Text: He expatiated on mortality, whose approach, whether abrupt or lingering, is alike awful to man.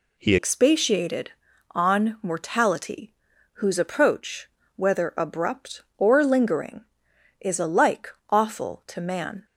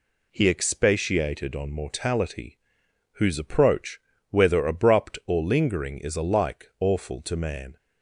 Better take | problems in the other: second | changes voice at "expatiated"; from 0.3 s on; 9.1 s long // pauses between "alike" and "awful"; slight; at 8.0 s; 0.20 s long

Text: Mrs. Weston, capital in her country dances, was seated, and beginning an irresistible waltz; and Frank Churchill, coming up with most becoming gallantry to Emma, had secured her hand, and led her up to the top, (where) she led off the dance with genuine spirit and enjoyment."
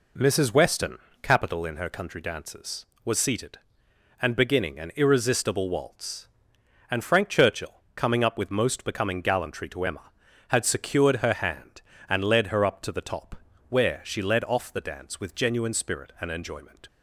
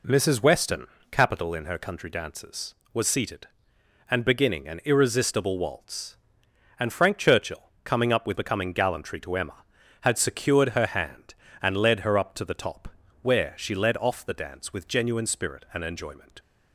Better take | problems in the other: first | skips "most"; at 8.3 s

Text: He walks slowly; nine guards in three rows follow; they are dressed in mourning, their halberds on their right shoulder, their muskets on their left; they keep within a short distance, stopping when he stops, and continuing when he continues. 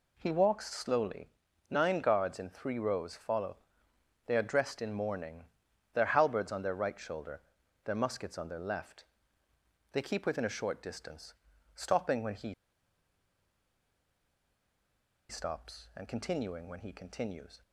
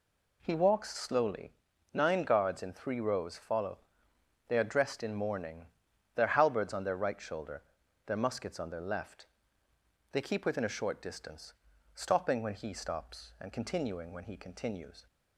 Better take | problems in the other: second | pauses between "he" and "stops"; strong; at 12.5 s; 2.7 s long

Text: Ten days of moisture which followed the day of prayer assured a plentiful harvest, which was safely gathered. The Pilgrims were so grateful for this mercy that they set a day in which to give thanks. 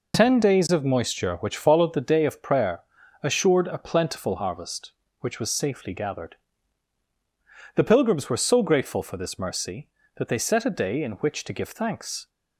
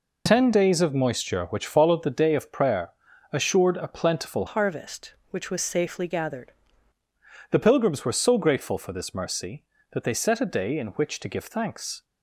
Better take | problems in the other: first | pauses between "prayer" and "assured"; at 2.8 s; 0.42 s long; also in the first // changes voice from "harvest" to "gathered"; from 4.4 to 6.5 s; 2.1 s long

